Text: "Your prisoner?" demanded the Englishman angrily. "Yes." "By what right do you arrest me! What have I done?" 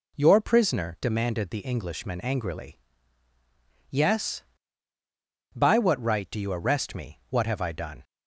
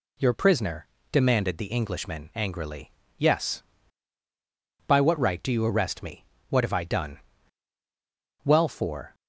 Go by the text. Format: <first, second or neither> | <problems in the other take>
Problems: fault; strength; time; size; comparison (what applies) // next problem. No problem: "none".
first | goes on to say "Well for"; noticeable; from 8.4 s on; 0.70 s long